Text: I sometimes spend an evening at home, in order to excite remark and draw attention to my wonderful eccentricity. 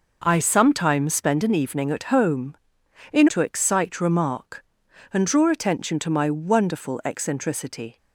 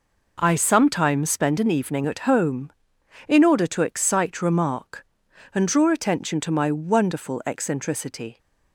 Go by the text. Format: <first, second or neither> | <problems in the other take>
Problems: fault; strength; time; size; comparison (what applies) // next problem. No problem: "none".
second | skips "order"; at 3.2 s